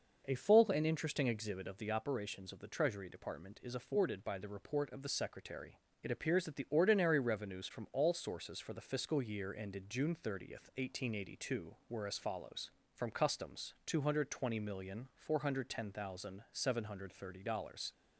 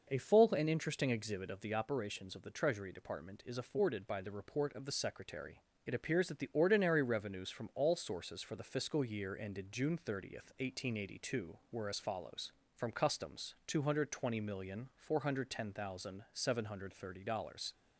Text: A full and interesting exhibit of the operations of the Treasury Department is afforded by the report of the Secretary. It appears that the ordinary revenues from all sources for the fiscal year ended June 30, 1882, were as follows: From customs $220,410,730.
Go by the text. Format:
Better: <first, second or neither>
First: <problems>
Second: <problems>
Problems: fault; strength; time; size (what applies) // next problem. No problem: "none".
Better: neither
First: none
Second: none